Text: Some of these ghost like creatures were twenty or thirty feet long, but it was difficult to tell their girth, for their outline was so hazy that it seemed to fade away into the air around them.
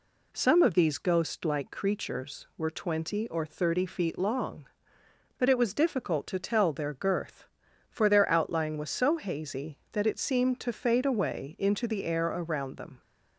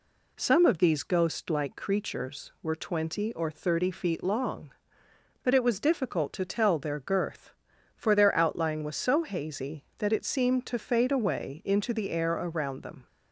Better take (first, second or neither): neither